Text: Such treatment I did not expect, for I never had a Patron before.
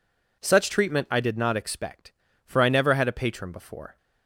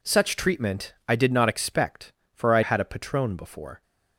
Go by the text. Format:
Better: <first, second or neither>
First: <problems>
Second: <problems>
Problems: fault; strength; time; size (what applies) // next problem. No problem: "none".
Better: first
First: none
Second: skips "never"; at 2.6 s